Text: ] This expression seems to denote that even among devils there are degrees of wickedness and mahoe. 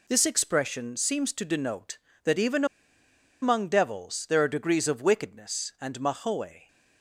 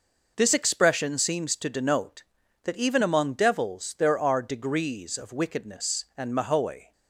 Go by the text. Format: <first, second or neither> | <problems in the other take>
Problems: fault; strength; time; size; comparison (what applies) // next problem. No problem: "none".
second | pauses between "even" and "among"; noticeable; at 2.6 s; 0.77 s long